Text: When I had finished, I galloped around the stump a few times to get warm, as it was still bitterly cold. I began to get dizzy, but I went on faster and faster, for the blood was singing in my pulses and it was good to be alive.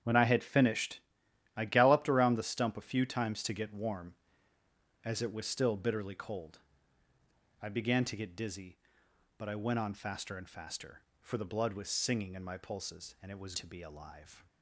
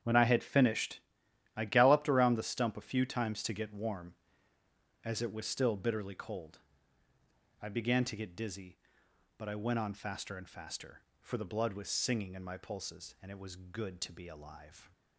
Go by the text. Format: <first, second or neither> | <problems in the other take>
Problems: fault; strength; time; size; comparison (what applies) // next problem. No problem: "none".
second | starts louder than the rest; strong; until 1.5 s; 9 dB; strong in the second // skips "good"; at 13.5 s